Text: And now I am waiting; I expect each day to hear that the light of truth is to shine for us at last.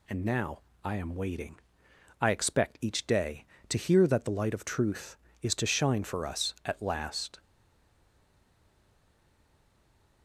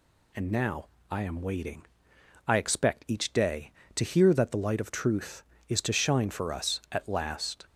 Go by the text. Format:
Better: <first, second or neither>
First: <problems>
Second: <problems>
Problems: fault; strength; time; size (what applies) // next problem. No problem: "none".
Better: second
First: pauses between "now" and "I"; slight; at 0.5 s; 0.24 s long // stays silent after the last word; strong; from 7.3 s on; 2.9 s long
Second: pauses between "now" and "I"; slight; at 0.8 s; 0.24 s long